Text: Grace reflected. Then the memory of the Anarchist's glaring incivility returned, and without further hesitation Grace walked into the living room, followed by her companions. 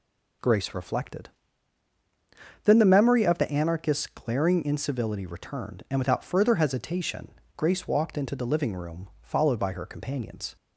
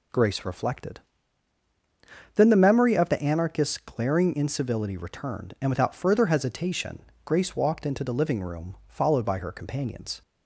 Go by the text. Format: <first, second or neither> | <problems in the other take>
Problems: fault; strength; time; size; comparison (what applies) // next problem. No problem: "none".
neither | pauses between "hesitation" and "Grace"; slight; the same in both